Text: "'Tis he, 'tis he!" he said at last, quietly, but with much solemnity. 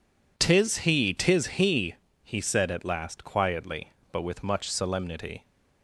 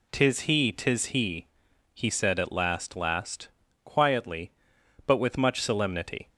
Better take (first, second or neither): first